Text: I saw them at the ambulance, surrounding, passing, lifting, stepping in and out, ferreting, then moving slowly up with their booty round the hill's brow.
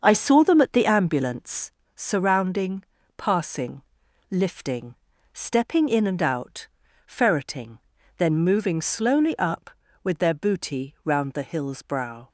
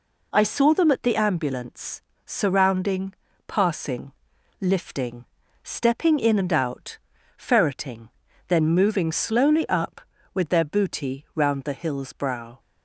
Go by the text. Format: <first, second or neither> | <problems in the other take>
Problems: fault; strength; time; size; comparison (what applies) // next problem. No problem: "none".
second | starts louder than the rest; until 1.8 s; 7 dB